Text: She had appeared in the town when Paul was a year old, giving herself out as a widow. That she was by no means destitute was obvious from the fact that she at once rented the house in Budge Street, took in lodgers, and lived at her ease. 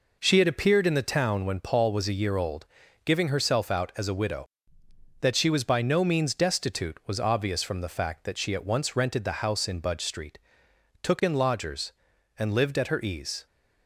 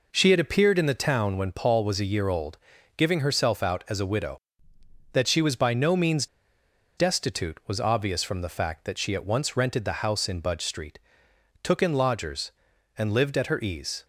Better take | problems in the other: first | pauses between "means" and "destitute"; noticeable; at 6.2 s; 0.70 s long

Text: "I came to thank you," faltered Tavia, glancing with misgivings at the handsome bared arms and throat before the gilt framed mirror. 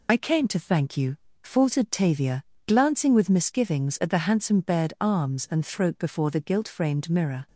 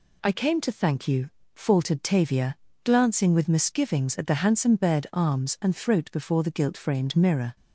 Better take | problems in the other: second | loses the start of "I"; at 0.0 s; 55 ms

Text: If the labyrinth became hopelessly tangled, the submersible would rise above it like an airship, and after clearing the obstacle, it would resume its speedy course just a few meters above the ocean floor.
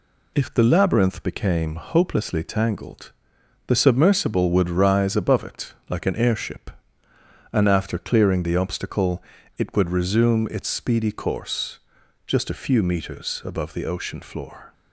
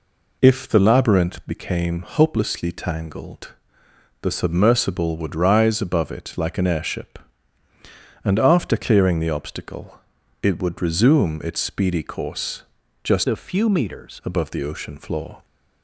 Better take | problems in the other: first | pauses between "course" and "just"; at 12.6 s; 0.42 s long; noticeable in the first // changes voice from "a" to "meters"; from 13.2 to 14.2 s; 1.0 s long

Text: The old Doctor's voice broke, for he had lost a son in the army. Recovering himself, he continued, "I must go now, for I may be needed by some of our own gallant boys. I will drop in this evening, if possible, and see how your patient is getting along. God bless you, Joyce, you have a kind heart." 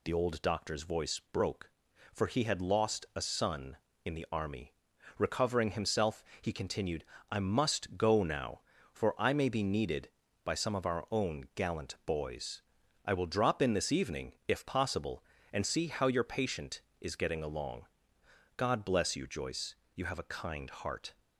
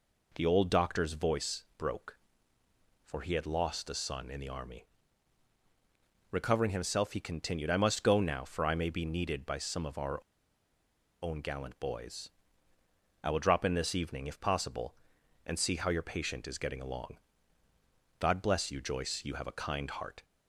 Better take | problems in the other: first | pauses between "our" and "own"; at 10.1 s; 1.0 s long

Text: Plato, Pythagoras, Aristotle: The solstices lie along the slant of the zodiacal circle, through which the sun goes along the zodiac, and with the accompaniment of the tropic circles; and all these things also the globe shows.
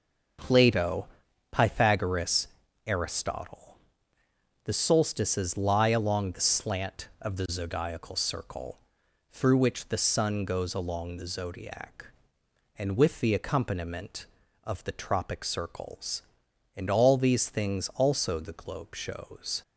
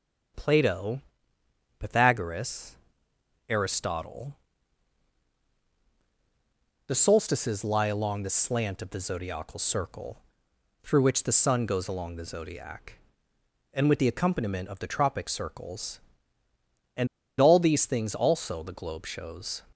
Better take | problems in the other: first | starts louder than the rest; strong; until 2.1 s; 8 dB; noticeable in the first // pauses between "and" and "all"; slight; at 17.0 s; 0.32 s long

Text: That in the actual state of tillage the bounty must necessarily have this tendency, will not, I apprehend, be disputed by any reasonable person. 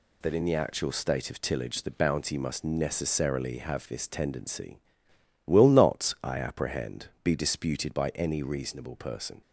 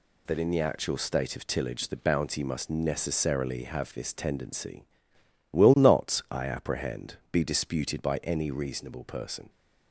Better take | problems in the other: neither | none

